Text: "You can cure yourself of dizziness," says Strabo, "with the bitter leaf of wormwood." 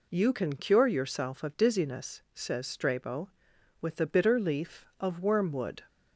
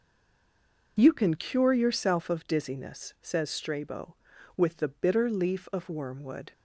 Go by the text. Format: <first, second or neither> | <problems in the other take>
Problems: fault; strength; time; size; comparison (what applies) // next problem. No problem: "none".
first | stays silent before the first word; slight; until 0.9 s; 0.9 s long